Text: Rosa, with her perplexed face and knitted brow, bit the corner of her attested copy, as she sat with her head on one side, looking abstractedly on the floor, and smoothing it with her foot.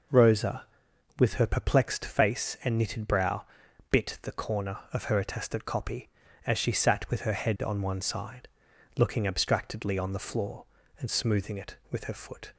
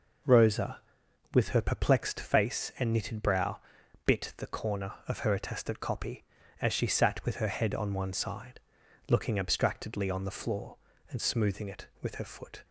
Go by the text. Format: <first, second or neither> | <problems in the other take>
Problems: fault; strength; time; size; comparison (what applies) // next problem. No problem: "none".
neither | none